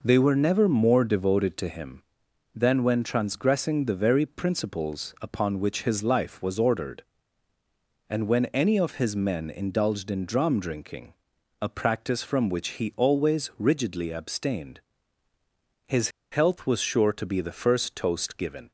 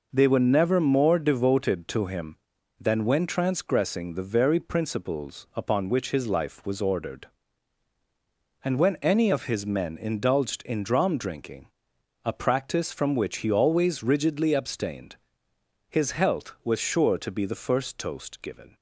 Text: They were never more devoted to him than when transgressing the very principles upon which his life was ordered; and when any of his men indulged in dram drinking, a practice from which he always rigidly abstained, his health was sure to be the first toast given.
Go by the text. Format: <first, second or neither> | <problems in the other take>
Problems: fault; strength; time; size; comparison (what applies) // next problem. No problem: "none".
second | pauses between "his" and "health"; slight; at 16.0 s; 0.22 s long